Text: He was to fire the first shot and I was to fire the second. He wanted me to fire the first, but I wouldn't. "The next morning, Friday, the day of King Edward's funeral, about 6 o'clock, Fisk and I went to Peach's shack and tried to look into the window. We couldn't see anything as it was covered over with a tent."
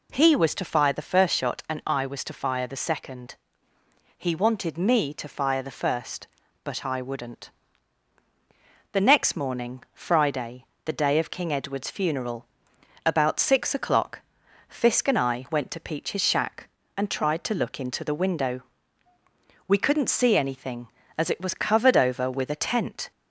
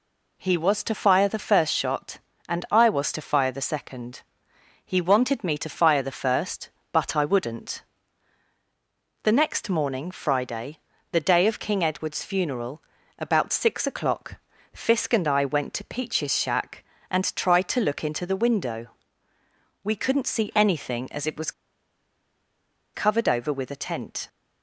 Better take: first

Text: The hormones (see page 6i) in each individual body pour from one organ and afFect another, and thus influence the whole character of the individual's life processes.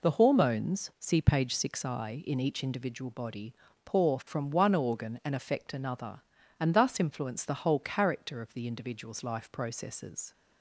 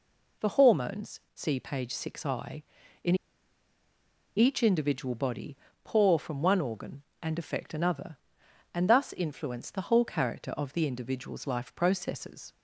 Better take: first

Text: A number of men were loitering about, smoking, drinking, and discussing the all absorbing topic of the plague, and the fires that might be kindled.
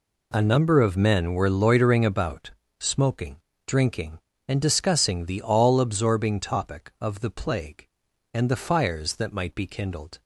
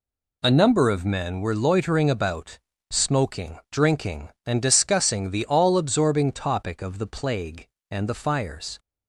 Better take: first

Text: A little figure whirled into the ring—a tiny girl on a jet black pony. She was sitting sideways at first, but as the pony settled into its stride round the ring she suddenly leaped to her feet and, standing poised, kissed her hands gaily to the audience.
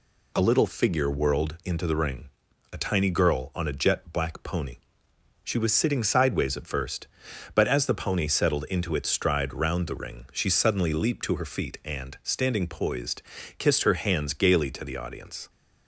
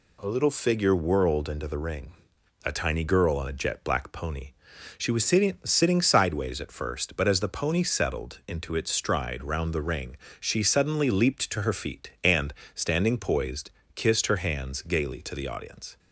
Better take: first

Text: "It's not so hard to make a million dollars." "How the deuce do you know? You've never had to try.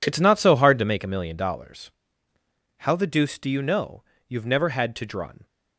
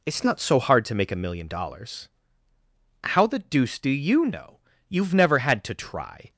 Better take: second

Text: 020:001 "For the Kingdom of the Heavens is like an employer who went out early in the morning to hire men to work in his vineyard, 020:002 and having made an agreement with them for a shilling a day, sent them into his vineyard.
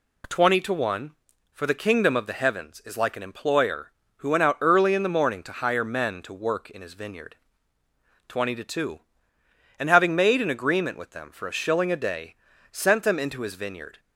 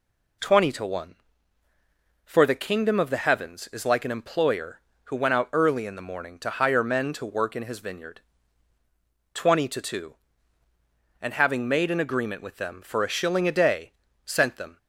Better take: first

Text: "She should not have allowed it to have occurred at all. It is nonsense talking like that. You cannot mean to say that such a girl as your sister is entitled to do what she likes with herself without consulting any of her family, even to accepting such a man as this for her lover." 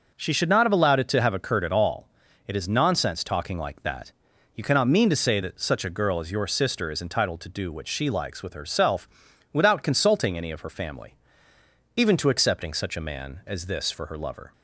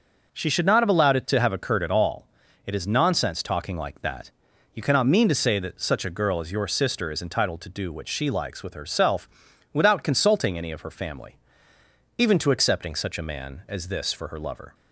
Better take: neither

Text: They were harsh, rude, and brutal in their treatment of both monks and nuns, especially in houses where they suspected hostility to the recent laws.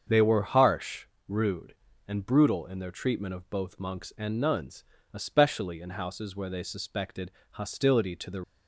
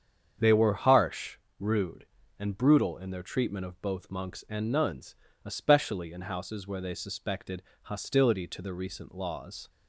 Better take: second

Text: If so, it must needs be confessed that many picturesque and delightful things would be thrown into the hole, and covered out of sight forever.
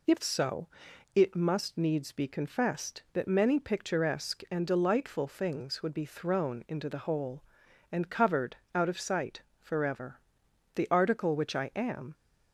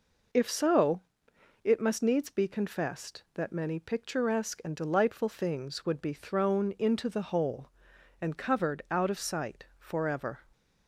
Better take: second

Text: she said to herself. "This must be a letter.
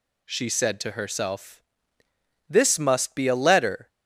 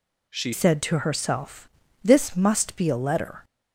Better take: first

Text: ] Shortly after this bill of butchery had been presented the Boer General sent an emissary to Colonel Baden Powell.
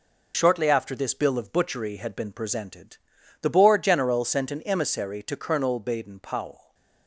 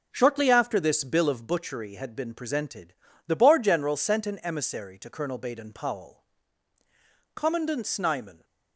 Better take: first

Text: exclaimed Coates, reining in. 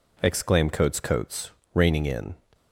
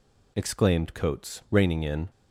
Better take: second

